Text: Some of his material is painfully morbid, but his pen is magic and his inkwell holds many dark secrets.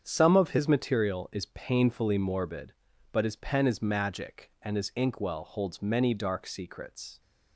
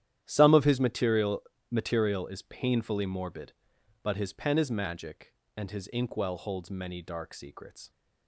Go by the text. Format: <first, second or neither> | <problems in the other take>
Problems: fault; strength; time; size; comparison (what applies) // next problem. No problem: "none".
first | starts louder than the rest; strong; until 1.2 s; 11 dB; strong in the first // says "material" twice; at 1.6 s